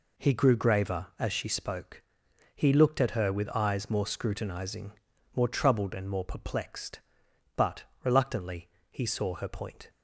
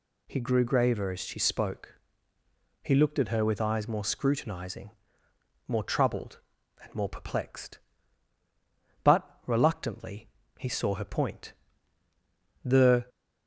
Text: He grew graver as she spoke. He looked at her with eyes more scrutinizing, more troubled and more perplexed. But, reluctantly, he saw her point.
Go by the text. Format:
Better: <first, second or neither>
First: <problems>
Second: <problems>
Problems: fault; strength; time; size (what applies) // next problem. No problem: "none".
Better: first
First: none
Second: goes on to say "The"; slight; from 12.6 s on; 0.42 s long